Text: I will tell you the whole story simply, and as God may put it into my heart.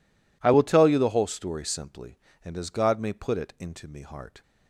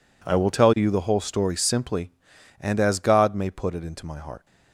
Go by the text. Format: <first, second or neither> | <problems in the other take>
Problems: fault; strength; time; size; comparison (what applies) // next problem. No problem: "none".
second | says "me" for "my"; at 3.8 s